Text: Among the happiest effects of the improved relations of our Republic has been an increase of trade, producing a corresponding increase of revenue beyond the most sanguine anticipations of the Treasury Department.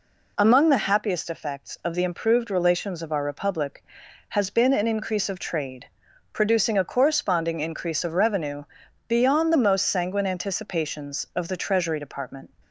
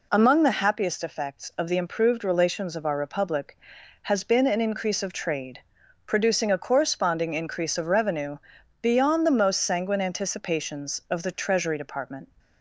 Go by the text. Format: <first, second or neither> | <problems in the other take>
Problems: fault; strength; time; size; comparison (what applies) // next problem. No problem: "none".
neither | pauses between "revenue" and "beyond"; the same in both